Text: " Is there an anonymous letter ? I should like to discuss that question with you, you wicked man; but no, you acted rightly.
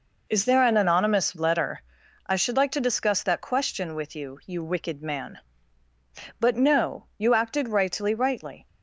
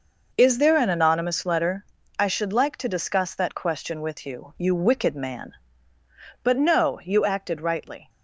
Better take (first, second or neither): second